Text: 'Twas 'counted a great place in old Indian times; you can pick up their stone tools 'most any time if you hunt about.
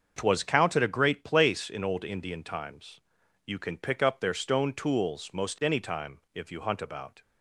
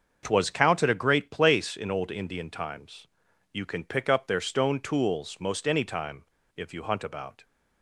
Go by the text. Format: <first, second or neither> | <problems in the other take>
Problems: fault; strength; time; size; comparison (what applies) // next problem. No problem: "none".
first | starts louder than the rest; until 1.2 s; 6.5 dB; also in the first // pauses between "time" and "if"; slight; at 6.2 s; 0.31 s long